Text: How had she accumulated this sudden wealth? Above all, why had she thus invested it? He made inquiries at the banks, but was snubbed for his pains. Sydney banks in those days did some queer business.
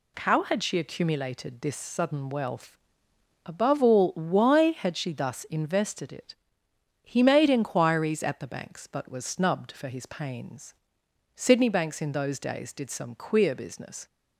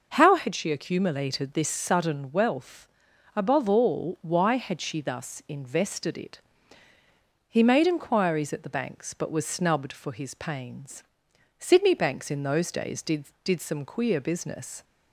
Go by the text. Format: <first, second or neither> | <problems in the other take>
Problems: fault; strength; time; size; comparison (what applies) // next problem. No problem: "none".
first | says "did" twice; at 13.4 s